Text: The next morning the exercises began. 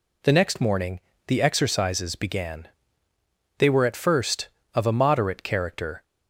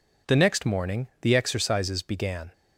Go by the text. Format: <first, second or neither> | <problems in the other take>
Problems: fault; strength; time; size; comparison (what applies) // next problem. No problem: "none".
second | pauses between "morning" and "the"; slight; at 0.9 s; 0.28 s long // goes on to say "They were at first of a moderate character"; strong; from 3.5 s on; 2.4 s long